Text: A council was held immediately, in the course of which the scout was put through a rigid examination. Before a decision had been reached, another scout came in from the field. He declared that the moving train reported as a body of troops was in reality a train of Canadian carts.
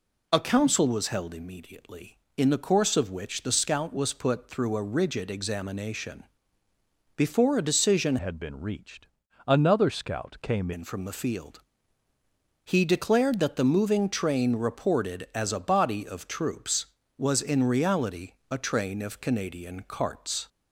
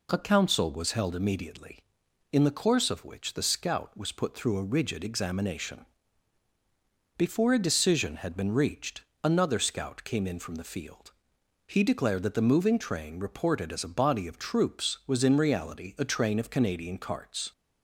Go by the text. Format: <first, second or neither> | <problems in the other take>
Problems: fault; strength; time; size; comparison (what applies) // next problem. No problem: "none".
second | changes voice from "had" to "came"; from 8.1 to 10.7 s; 2.6 s long // pauses between "reality" and "a"; slight; at 18.3 s; 0.16 s long